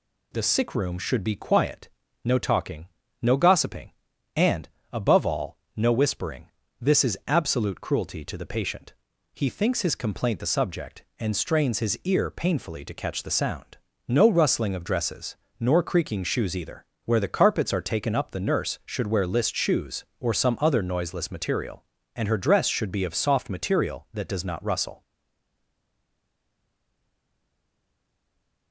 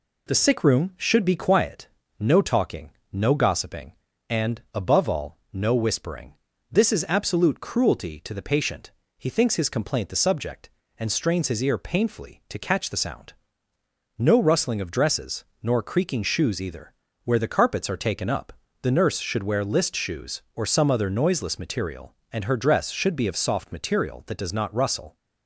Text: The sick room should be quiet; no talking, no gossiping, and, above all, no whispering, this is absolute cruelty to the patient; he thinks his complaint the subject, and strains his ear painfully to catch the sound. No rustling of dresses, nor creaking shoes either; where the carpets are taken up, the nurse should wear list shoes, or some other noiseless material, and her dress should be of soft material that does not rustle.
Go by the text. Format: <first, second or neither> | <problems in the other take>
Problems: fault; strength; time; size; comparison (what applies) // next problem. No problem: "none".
second | stays silent after the last word; strong; from 25.0 s on; 3.7 s long